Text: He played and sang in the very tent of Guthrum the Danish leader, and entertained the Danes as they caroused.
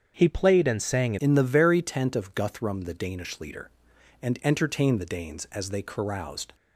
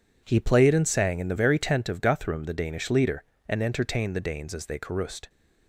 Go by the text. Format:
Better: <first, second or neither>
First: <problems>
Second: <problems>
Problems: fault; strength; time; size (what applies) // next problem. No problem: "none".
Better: second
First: starts louder than the rest; strong; until 1.1 s; 7 dB // changes voice at "in"; from 1.1 s on; 5.4 s long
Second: none